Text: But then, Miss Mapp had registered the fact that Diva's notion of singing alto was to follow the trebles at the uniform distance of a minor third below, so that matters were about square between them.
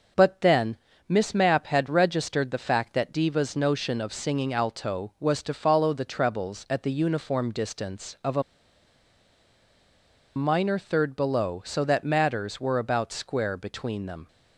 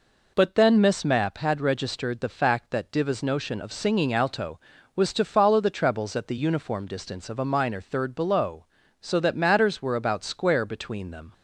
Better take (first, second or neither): second